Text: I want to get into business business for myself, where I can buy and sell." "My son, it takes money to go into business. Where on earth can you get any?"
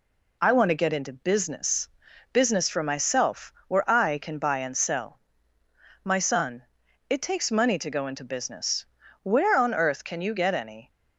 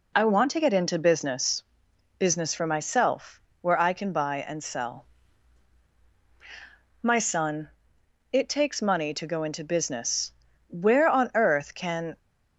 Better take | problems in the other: first | pauses between "business" and "business"; noticeable; at 1.6 s; 0.56 s long; noticeable in the first // stops before "you get any"; at 12.1 s

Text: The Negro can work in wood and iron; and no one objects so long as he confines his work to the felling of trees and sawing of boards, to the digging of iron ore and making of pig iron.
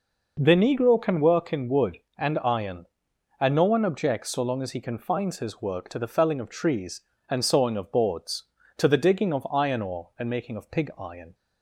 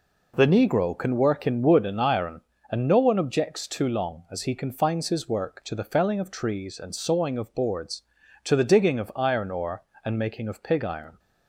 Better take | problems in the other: first | says "too" for "so"; at 3.6 s

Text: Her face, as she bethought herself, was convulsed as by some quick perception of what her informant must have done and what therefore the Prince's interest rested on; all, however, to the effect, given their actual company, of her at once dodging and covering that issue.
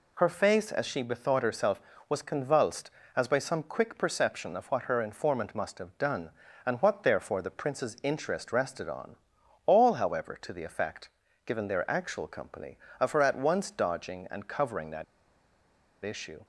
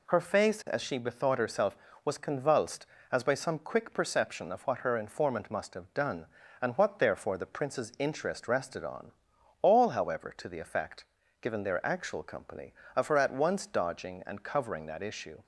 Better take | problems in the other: second | pauses between "that" and "issue"; at 15.0 s; 1.0 s long

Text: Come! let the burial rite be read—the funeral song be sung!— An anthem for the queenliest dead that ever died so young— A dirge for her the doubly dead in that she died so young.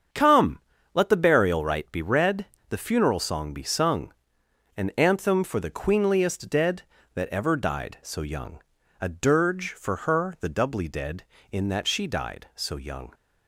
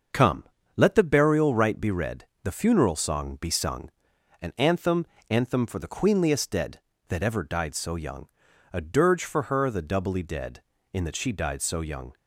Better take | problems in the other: first | starts louder than the rest; until 1.4 s; 6.5 dB; also in the first // says "anthem" twice; at 5.2 s

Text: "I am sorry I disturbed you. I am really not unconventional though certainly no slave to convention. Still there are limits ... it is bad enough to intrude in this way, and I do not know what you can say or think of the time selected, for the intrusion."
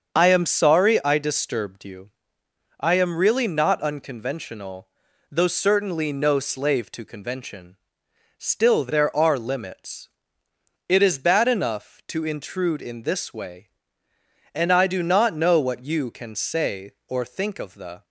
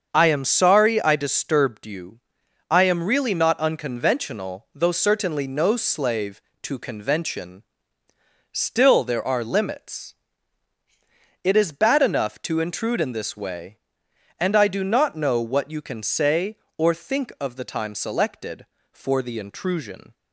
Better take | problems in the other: second | starts louder than the rest; until 1.1 s; 7 dB; also in the second // pauses between "unconventional" and "though"; at 4.8 s; 0.44 s long // stops before "time selected for the intrusion"; at 18.0 s

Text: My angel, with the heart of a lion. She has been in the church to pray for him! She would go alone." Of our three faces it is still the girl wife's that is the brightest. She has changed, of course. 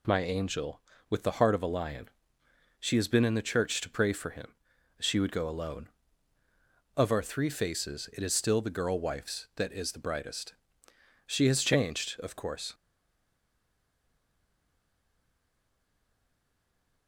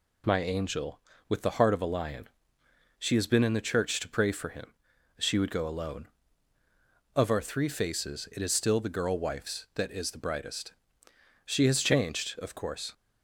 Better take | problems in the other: second | stays silent after the last word; strong; from 12.7 s on; 4.3 s long

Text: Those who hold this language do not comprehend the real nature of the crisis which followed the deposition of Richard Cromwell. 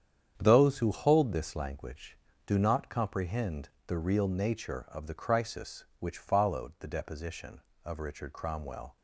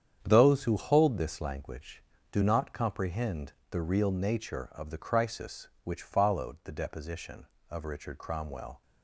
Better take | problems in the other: neither | starts louder than the rest; strong; the same in both // pauses between "comprehend" and "the"; slight; the same in both

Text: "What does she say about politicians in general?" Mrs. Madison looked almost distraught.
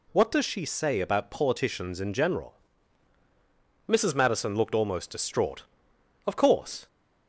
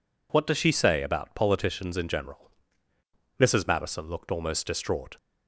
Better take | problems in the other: second | goes on to say "Of course"; noticeable; from 6.2 s on; 0.62 s long

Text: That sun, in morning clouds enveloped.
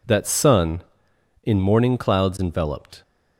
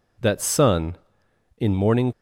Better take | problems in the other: first | stops before "clouds enveloped"; at 2.1 s

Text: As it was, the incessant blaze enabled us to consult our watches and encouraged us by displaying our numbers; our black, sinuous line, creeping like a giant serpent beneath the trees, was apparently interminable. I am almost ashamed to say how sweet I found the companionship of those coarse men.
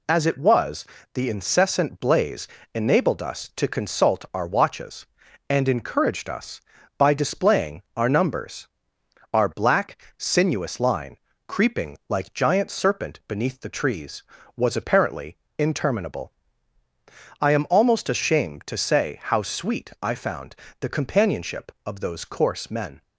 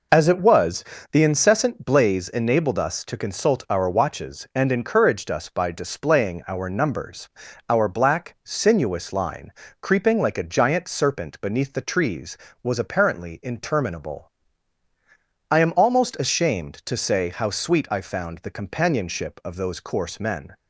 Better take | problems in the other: second | pauses between "blaze" and "enabled"; slight; at 2.4 s; 0.28 s long // pauses between "displaying" and "our"; slight; at 7.8 s; 0.16 s long // skips "a"; at 12.3 s // pauses between "apparently" and "interminable"; slight; at 15.3 s; 0.20 s long // pauses between "found" and "the"; slight; at 20.5 s; 0.26 s long

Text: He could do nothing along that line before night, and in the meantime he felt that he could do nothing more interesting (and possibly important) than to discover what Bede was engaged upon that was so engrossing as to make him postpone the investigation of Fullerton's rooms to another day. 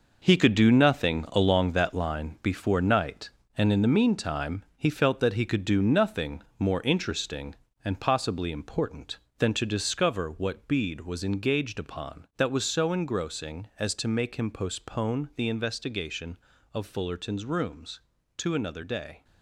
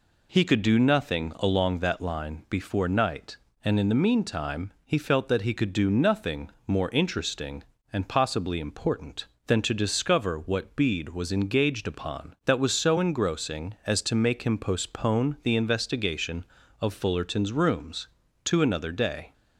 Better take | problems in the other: second | gets quieter; strong; throughout; 9.5 dB // pauses between "nothing" and "more"; slight; at 6.4 s; 0.16 s long; slight in the second

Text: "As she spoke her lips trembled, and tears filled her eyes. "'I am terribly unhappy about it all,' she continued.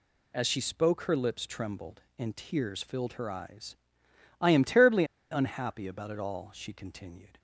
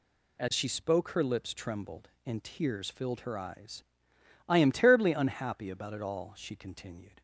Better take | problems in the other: second | pauses between "terribly" and "unhappy"; slight; at 5.0 s; 0.27 s long

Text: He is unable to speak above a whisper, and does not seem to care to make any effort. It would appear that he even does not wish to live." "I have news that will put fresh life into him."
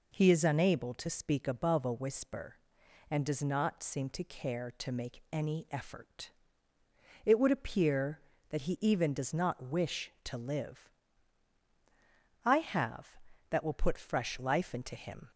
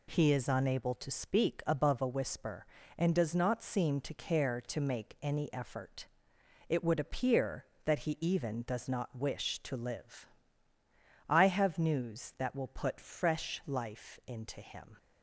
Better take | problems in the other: second | skips "news"; at 13.3 s

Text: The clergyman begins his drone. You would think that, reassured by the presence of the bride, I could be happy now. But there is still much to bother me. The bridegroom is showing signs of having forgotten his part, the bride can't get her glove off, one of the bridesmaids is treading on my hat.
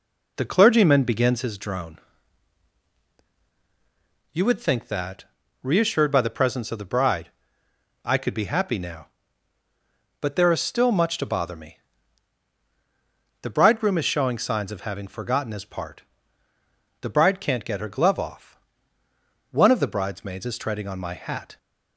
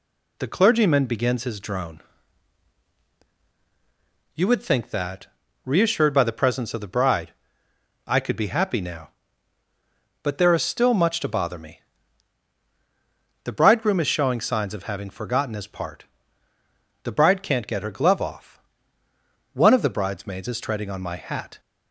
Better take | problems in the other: second | starts louder than the rest; until 1.6 s; 3.5 dB

